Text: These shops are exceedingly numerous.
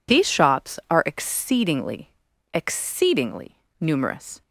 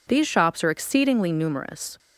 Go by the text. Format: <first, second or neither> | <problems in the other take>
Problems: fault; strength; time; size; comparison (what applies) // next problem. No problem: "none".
second | says "exceedingly" twice; at 2.5 s